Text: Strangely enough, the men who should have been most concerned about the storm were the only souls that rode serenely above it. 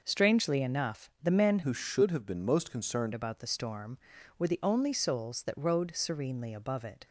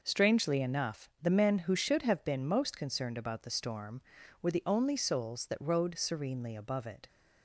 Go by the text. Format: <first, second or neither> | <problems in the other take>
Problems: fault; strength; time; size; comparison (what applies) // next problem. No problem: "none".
second | changes voice from "who" to "concerned"; from 1.6 to 3.1 s; 1.5 s long